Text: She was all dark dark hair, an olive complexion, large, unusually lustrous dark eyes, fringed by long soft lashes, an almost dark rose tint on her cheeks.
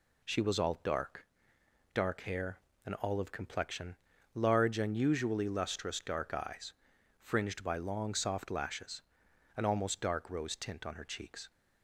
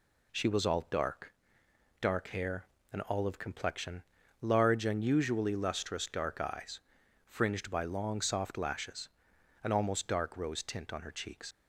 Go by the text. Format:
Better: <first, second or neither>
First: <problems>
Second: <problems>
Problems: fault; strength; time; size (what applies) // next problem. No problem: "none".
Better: first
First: pauses between "dark" and "dark"; noticeable; at 1.2 s; 0.68 s long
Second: pauses between "dark" and "dark"; noticeable; at 1.3 s; 0.68 s long // leaves "cheeks" unfinished; at 11.5 s; 65 ms